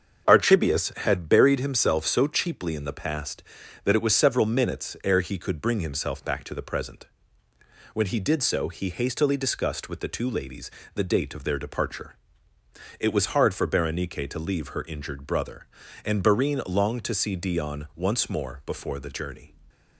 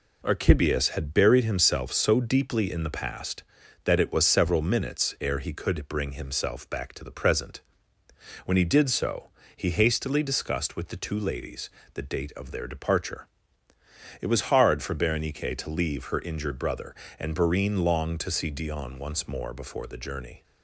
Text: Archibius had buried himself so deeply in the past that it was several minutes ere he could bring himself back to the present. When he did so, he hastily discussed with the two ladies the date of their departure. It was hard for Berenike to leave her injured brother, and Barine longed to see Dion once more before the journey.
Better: second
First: starts louder than the rest; until 1.2 s; 6.5 dB // says "cheaply" for "deeply"; at 2.2 s // pauses between "ladies" and "the"; slight; at 10.7 s; 0.24 s long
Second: pauses between "ladies" and "the"; slight; at 11.6 s; 0.24 s long

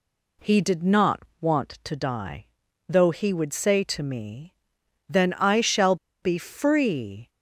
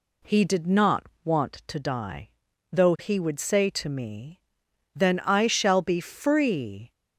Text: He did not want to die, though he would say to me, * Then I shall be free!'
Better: second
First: pauses between "not" and "want"; slight; at 1.2 s; 0.18 s long // pauses between "shall" and "be"; slight; at 5.9 s; 0.26 s long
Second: pauses between "not" and "want"; slight; at 1.0 s; 0.18 s long

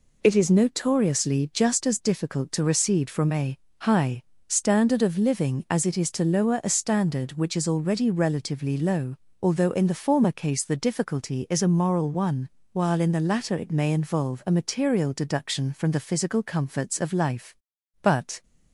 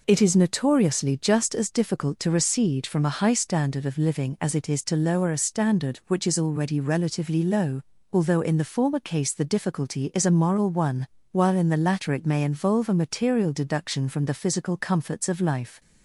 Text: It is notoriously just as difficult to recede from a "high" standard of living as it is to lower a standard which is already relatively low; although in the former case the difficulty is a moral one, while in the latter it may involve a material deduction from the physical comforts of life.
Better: second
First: pauses between "a" and "high"; slight; at 3.5 s; 0.20 s long // pauses between "high" and "standard"; slight; at 4.2 s; 0.26 s long // goes on to say "But"; slight; from 18.0 s on; 0.40 s long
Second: none

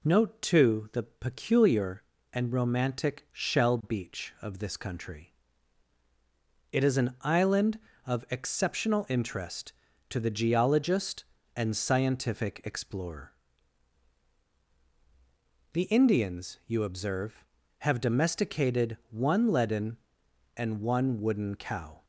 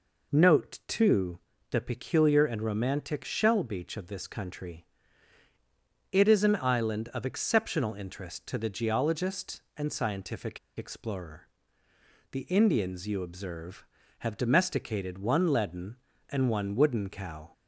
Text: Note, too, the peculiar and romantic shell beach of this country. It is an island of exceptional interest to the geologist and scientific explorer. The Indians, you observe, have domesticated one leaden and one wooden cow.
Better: first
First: none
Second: pauses between "scientific" and "explorer"; slight; at 10.5 s; 0.19 s long

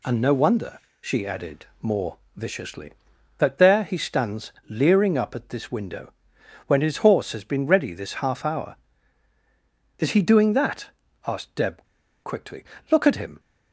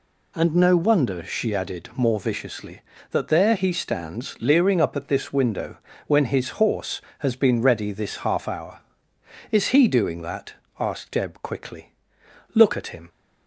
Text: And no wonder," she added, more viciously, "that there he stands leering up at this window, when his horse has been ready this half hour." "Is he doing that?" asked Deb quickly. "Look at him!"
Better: second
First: pauses between "more" and "viciously"; slight; at 2.1 s; 0.20 s long // pauses between "stands" and "leering"; slight; at 4.5 s; 0.16 s long // pauses between "Deb" and "quickly"; at 11.8 s; 0.39 s long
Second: none

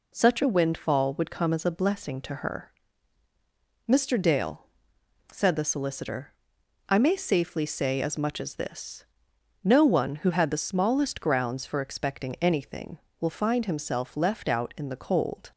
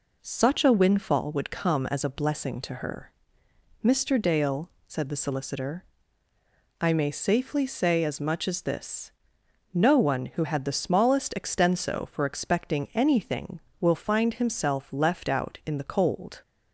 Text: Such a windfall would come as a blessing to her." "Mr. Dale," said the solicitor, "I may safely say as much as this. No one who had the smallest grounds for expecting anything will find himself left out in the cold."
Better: first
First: none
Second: says "extenso" for "grounds"; at 11.3 s

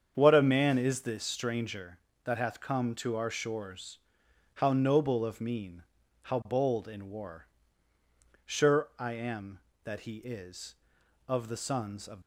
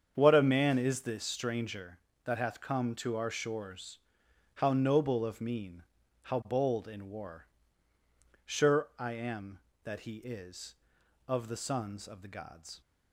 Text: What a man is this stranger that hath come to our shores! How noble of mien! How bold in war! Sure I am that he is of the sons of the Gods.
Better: second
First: starts louder than the rest; strong; until 1.1 s; 7.5 dB // stops before "the Gods"; at 12.2 s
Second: starts louder than the rest; strong; until 1.1 s; 7.5 dB

